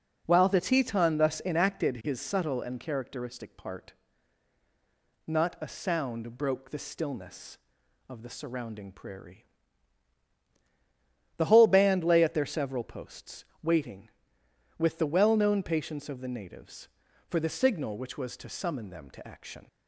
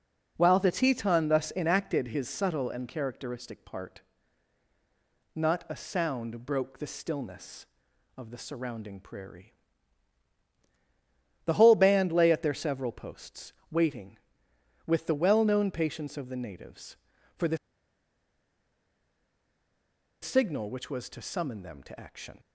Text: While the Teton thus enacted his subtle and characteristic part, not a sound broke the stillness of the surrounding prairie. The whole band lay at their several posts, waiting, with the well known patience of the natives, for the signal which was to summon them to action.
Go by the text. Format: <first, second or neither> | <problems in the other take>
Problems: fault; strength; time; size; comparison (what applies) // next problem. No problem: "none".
first | pauses between "the" and "signal"; strong; at 17.5 s; 2.6 s long